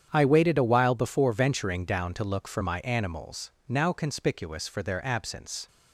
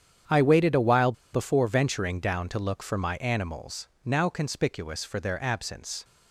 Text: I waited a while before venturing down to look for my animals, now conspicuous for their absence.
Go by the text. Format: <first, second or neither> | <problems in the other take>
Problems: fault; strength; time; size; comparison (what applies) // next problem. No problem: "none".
first | starts louder than the rest; strong; until 1.4 s; 8.5 dB; strong in the first // pauses between "while" and "before"; slight; at 1.1 s; 0.21 s long